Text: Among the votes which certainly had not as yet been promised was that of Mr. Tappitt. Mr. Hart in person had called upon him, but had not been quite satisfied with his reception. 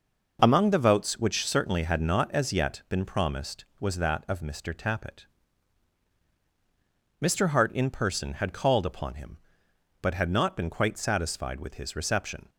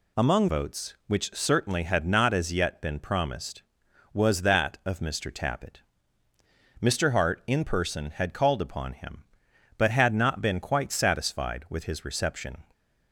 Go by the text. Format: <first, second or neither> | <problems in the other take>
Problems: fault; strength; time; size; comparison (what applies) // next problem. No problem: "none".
first | skips "the"; at 0.4 s